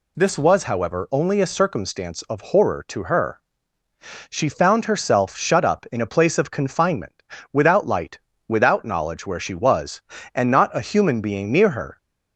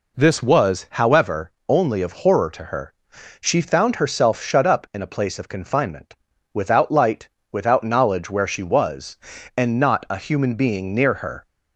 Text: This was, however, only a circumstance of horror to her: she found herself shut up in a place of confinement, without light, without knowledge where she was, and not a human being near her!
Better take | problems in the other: first | skips "a circumstance"; at 2.0 s

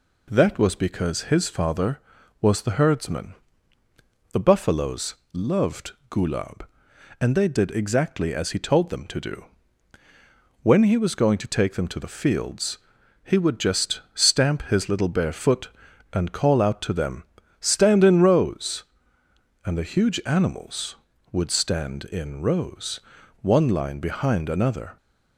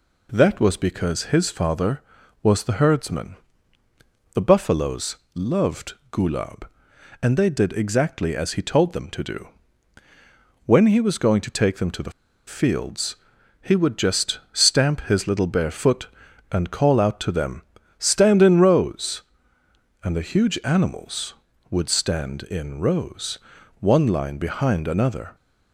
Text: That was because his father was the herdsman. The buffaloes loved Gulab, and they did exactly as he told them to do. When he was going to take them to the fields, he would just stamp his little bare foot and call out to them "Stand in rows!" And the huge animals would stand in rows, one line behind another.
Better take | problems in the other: first | pauses between "buffaloes" and "loved"; slight; at 5.1 s; 0.18 s long; slight in the first // pauses between "loved" and "Gulab"; slight; at 5.9 s; 0.18 s long; slight in the first // pauses between "the" and "fields"; slight; at 12.1 s; 0.34 s long // pauses between "them" and "Stand"; at 17.6 s; 0.38 s long; also in the first

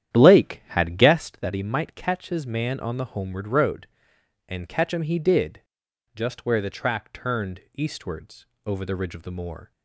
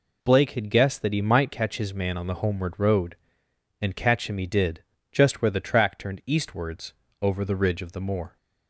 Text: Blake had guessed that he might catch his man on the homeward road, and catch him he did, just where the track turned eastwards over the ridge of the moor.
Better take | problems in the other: second | starts louder than the rest; strong; until 1.4 s; 10.5 dB // pauses between "eastwards" and "over"; slight; at 8.4 s; 0.20 s long; slight in the second

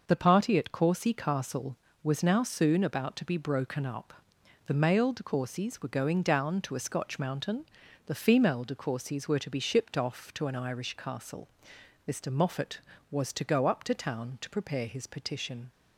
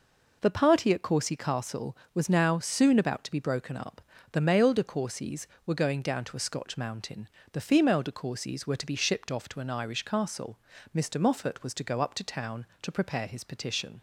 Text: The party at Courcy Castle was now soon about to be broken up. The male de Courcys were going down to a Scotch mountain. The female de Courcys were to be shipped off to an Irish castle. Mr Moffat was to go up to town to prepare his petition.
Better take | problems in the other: neither | none

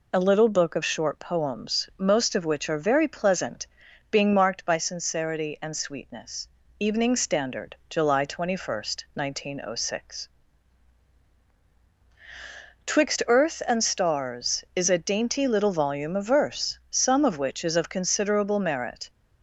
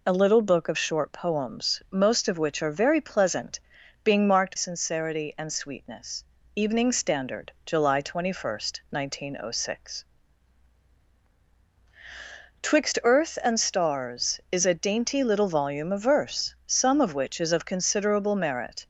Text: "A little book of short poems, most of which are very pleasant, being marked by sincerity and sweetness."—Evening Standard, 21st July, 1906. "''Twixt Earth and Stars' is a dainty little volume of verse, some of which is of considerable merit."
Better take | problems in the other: first | skips "by"; at 4.5 s

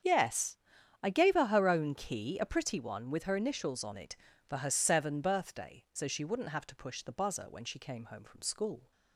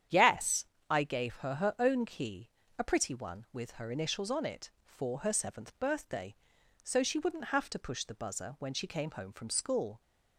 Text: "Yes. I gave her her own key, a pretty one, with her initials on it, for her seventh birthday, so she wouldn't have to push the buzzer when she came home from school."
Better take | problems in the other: second | starts louder than the rest; strong; until 1.4 s; 8 dB; strong in the second // says "seven" for "seventh"; at 4.7 s

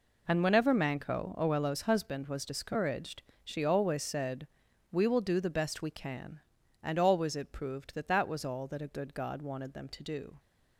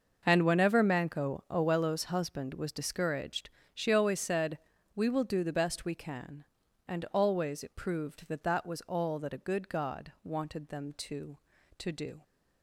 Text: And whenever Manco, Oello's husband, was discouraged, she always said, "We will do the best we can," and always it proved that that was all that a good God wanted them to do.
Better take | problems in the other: first | starts louder than the rest; noticeable; until 1.2 s; 6 dB // says "to" twice; at 11.7 s

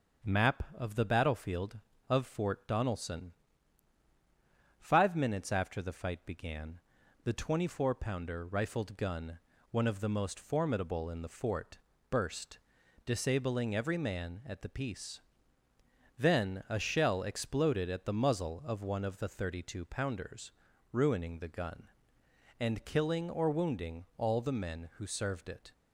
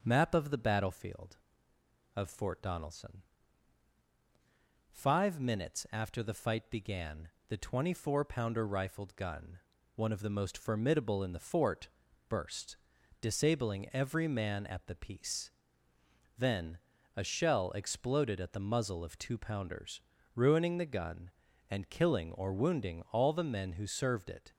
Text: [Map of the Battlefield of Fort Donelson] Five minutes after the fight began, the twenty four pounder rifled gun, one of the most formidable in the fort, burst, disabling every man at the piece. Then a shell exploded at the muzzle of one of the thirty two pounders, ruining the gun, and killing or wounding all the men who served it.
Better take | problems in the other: first | starts louder than the rest; until 1.0 s; 6.5 dB; also in the first // pauses between "Donelson" and "Five"; strong; at 3.2 s; 1.6 s long; strong in the first // pauses between "Then" and "a"; slight; at 16.7 s; 0.36 s long // skips "one of the thirty"; at 19.1 s

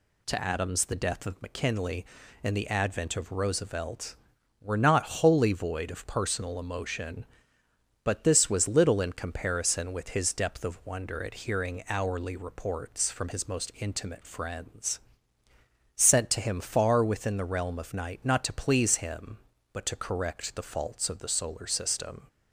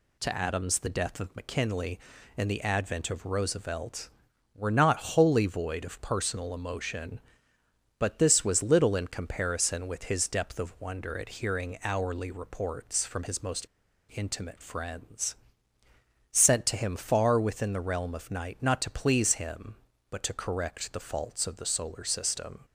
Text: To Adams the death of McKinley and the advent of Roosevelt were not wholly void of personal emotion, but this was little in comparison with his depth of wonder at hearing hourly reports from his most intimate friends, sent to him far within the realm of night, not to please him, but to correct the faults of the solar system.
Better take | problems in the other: first | pauses between "most" and "intimate"; at 13.6 s; 0.43 s long

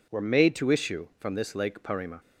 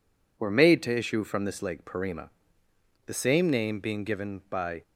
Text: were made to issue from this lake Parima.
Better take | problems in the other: first | goes on to say "The same name being given by"; strong; from 3.0 s on; 1.7 s long

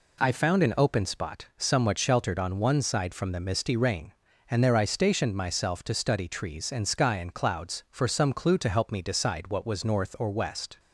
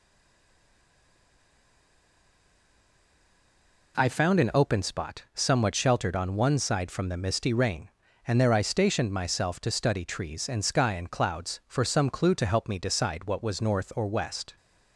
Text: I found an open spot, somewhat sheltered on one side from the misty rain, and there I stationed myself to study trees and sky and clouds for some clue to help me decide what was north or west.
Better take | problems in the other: first | stays silent before the first word; strong; until 3.9 s; 3.9 s long

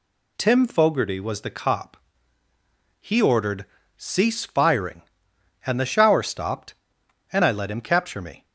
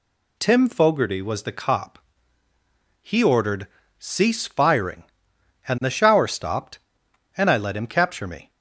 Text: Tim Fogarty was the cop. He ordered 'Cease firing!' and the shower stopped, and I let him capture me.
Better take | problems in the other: neither | pauses between "ordered" and "Cease"; slight; the same in both

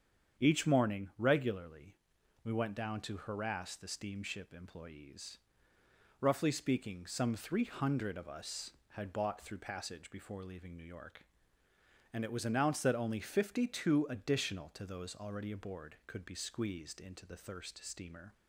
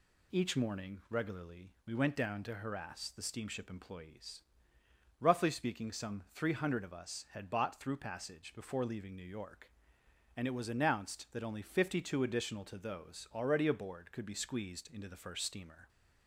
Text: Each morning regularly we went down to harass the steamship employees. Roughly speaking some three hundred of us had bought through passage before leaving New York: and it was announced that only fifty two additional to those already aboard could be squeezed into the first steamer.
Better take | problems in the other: second | starts louder than the rest; strong; until 1.4 s; 8 dB // pauses between "regularly" and "we"; noticeable; at 1.9 s; 0.50 s long // says "thirst" for "first"; at 17.3 s

